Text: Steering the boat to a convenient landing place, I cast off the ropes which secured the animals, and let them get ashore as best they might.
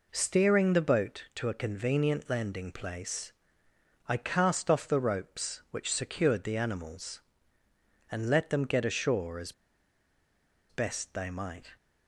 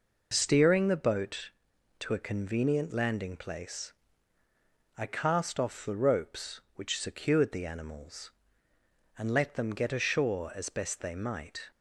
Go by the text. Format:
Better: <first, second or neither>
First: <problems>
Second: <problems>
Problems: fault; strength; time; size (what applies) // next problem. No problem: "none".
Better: second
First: pauses between "as" and "best"; at 9.5 s; 1.1 s long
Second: none